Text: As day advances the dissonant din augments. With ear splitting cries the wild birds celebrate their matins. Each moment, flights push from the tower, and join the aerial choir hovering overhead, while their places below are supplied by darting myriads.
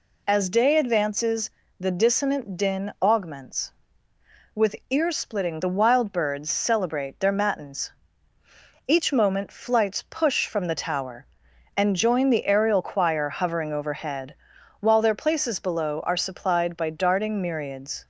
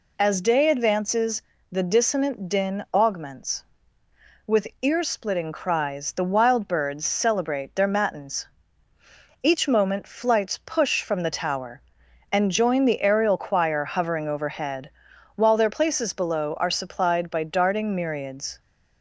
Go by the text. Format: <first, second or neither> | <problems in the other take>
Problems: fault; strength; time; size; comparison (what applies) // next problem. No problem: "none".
second | pauses between "advances" and "the"; slight; at 1.4 s; 0.32 s long; slight in the second // pauses between "With" and "ear"; slight; at 4.7 s; 0.16 s long; slight in the second // skips "cries"; at 5.5 s